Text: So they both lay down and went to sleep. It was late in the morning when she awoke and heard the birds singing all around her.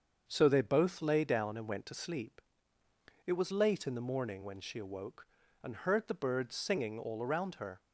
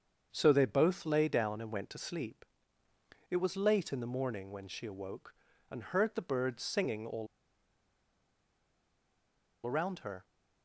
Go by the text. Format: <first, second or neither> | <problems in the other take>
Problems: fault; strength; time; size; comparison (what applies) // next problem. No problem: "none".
first | starts louder than the rest; until 1.3 s; 7 dB; also in the first // pauses between "all" and "around"; strong; at 7.2 s; 2.3 s long